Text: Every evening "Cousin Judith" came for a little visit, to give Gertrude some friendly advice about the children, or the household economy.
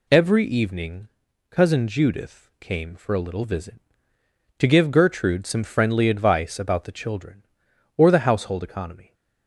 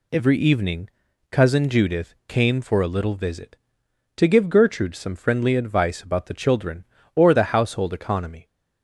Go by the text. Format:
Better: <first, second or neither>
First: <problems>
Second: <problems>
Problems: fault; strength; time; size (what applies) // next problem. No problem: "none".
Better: neither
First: pauses between "evening" and "Cousin"; at 1.0 s; 0.40 s long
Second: pauses between "evening" and "Cousin"; at 0.8 s; 0.40 s long